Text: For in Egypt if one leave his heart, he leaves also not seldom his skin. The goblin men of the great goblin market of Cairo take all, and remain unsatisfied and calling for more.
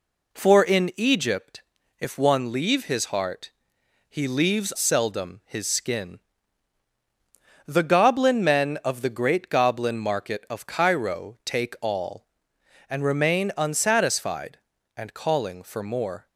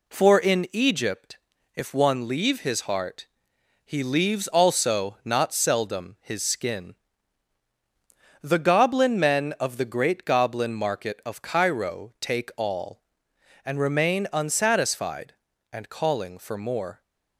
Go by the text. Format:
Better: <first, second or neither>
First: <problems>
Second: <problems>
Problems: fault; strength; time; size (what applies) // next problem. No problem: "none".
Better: second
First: pauses between "Egypt" and "if"; at 1.6 s; 0.38 s long // skips "also not"; at 4.7 s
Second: pauses between "Egypt" and "if"; at 1.3 s; 0.38 s long